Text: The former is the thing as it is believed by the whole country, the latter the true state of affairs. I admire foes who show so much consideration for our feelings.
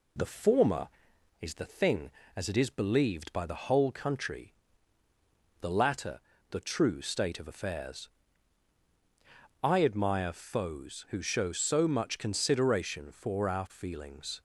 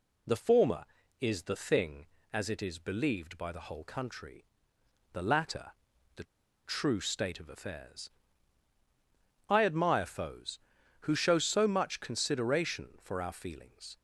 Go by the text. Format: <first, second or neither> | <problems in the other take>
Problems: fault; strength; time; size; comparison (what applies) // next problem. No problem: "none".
first | pauses between "latter" and "the"; at 5.7 s; 0.42 s long; slight in the first // pauses between "the" and "true"; at 6.2 s; 0.41 s long